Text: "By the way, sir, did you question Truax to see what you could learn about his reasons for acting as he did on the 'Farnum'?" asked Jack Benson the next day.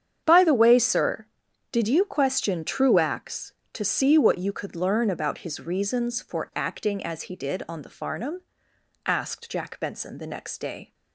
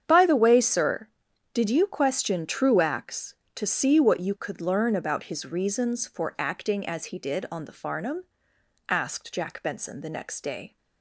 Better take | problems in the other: neither | starts louder than the rest; strong; the same in both

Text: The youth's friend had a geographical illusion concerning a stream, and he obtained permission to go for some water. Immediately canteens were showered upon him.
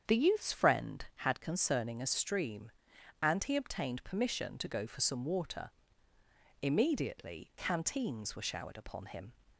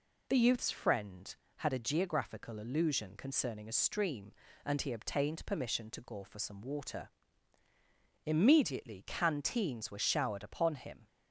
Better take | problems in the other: second | starts louder than the rest; strong; until 1.2 s; 7.5 dB // skips "a geographical illusion"; at 1.3 s

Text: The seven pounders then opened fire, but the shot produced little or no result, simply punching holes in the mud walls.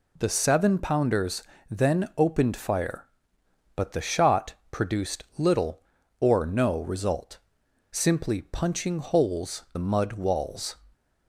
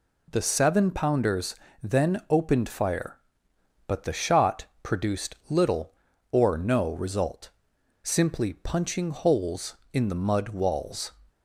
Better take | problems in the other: second | pauses between "pounders" and "then"; slight; at 1.4 s; 0.26 s long; slight in the second // pauses between "shot" and "produced"; slight; at 4.5 s; 0.16 s long; slight in the second // skips "in"; at 9.6 s

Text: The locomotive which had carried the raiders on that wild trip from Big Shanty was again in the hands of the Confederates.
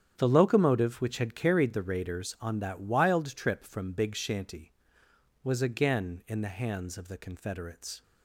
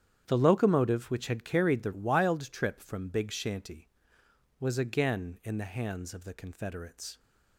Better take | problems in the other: first | starts louder than the rest; strong; until 1.2 s; 9 dB; strong in the first // skips "raiders on that"; at 1.9 s

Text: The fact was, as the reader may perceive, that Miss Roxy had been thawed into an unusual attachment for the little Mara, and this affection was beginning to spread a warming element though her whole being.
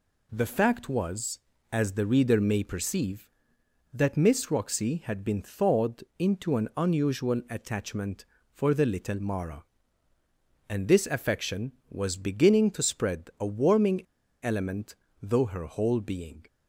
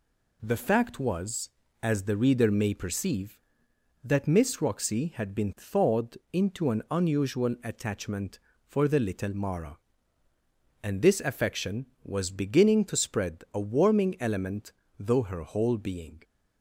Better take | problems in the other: second | pauses between "thawed" and "into"; slight; at 6.0 s; 0.16 s long; slight in the second // pauses between "warming" and "element"; at 14.0 s; 0.38 s long // pauses between "element" and "though"; slight; at 14.9 s; 0.26 s long; slight in the second

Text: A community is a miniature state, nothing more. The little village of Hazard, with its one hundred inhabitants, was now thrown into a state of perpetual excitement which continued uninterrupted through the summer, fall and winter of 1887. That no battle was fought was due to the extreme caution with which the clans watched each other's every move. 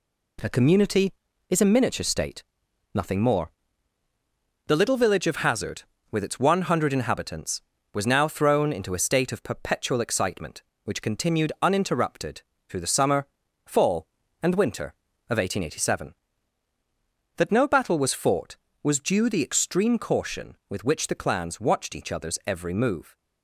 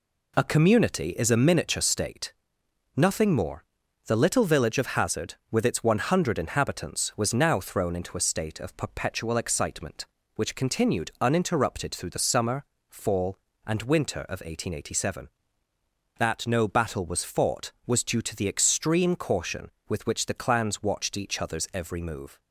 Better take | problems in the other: second | pauses between "uninterrupted" and "through"; slight; at 12.4 s; 0.28 s long // skips "to"; at 19.2 s

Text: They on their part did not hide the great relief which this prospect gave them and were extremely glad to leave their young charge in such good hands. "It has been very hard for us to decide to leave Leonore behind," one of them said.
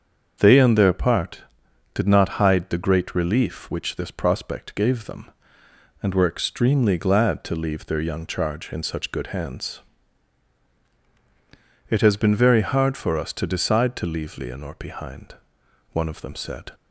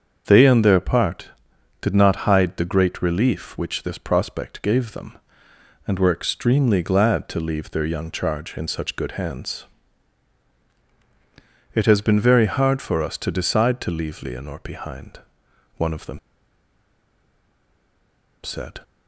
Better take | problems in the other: first | starts louder than the rest; until 1.2 s; 7 dB; also in the first // pauses between "them" and "said"; strong; at 16.1 s; 2.2 s long

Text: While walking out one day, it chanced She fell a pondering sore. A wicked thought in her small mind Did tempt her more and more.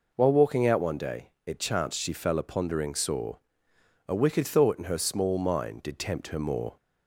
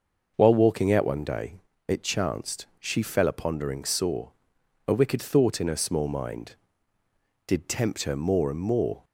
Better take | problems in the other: second | stops before "and more"; at 6.7 s

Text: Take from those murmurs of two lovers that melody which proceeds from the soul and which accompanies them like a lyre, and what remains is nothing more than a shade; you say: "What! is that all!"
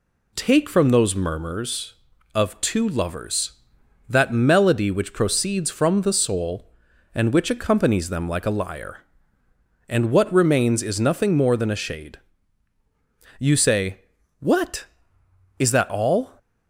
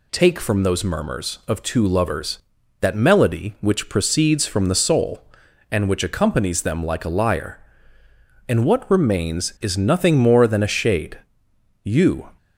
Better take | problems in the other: first | stops before "say What is that all"; at 12.3 s

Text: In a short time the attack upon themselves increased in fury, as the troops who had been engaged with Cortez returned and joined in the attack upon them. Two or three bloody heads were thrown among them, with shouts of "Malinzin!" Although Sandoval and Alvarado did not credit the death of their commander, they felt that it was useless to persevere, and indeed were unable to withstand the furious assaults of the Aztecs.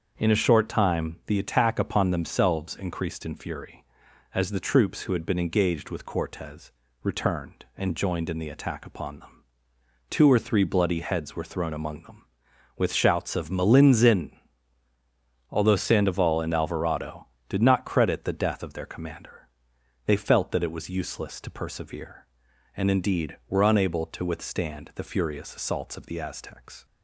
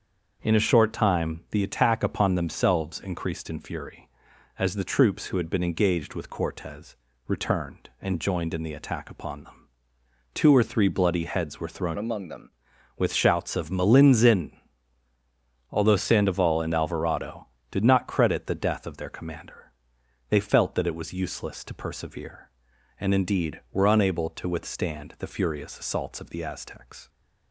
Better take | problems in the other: first | starts louder than the rest; until 1.5 s; 7 dB; also in the first // pauses between "Cortez" and "returned"; slight; at 6.9 s; 0.30 s long; slight in the first // changes voice from "among" to "them"; from 11.9 to 12.5 s; 0.6 s long

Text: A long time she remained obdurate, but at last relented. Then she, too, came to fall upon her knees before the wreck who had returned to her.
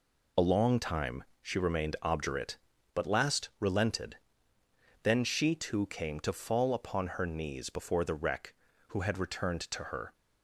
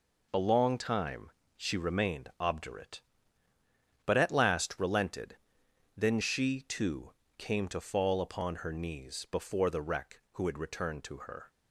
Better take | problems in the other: second | pauses between "time" and "she"; slight; at 1.2 s; 0.18 s long; slight in the second // skips "at"; at 3.0 s

